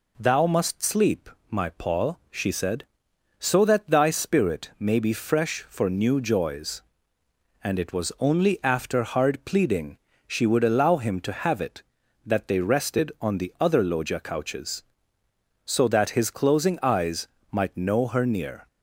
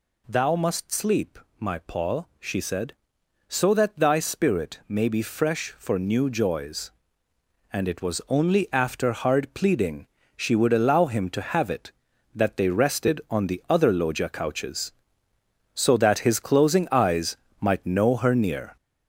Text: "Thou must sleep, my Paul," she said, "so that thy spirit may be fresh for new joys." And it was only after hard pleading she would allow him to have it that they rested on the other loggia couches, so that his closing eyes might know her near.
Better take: first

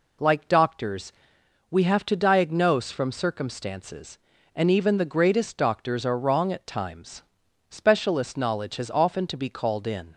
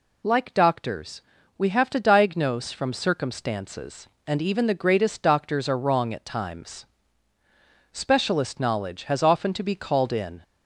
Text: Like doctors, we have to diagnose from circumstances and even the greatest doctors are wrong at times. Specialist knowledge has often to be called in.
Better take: neither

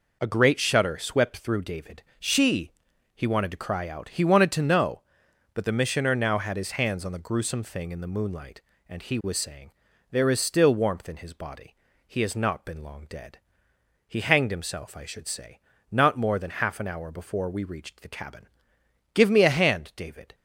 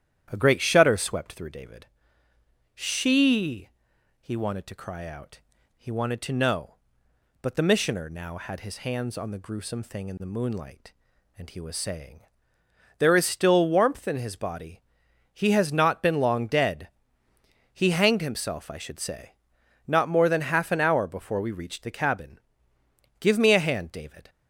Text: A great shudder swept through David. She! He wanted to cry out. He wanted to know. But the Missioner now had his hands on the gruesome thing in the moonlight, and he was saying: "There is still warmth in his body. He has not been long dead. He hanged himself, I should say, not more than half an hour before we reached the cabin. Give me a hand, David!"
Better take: first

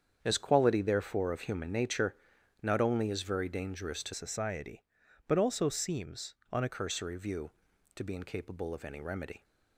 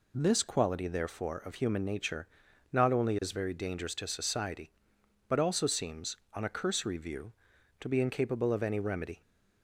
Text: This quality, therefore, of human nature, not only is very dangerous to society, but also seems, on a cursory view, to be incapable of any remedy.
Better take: second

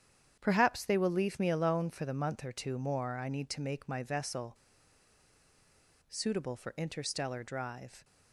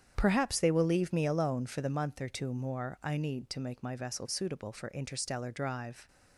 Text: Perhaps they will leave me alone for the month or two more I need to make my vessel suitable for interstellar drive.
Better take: second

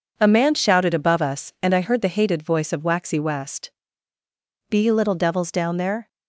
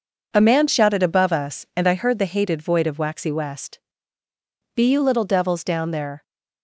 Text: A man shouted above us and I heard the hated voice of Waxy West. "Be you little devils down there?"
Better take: first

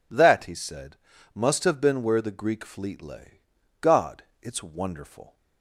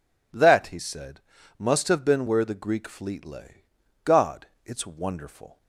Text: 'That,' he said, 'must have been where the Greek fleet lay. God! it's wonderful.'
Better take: neither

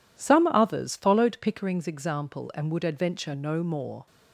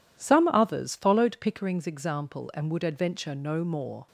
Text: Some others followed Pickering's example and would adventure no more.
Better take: neither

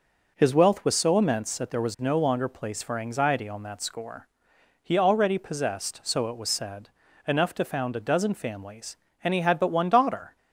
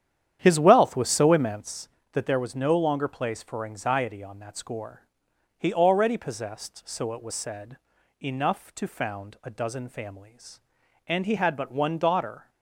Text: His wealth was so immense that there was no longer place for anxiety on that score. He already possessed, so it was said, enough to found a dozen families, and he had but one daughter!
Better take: first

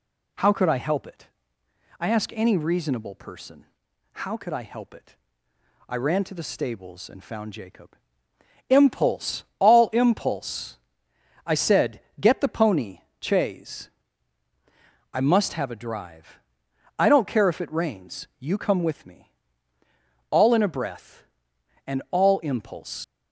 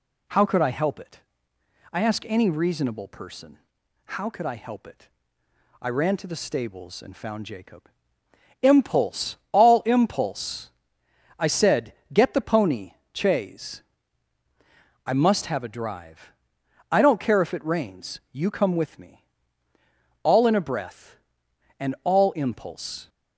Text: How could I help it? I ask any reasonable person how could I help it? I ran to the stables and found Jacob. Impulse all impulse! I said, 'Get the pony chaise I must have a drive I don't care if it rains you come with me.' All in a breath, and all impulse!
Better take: second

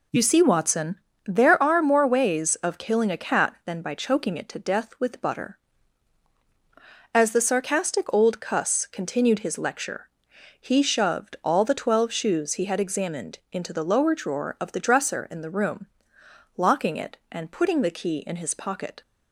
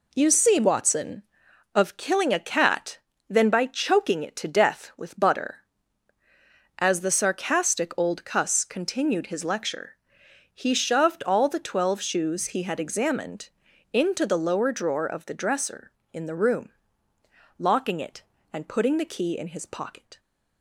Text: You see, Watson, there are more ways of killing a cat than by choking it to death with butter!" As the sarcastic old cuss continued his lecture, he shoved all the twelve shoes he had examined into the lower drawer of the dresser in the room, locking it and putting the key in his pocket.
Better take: first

